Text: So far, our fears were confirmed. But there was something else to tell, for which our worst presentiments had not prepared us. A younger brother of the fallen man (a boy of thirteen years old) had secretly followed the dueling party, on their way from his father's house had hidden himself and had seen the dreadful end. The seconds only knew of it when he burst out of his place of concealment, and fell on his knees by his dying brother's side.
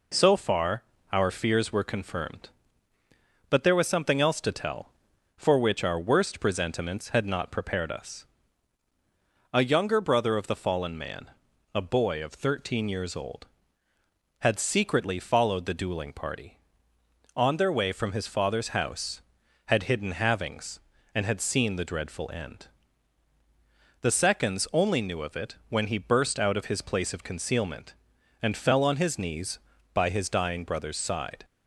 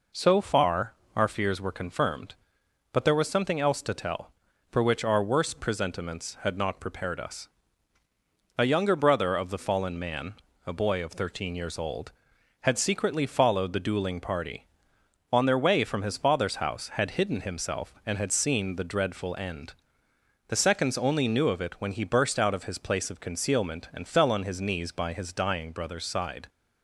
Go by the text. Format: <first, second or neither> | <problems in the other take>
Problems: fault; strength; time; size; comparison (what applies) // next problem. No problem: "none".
second | says "havings" for "himself"; at 20.1 s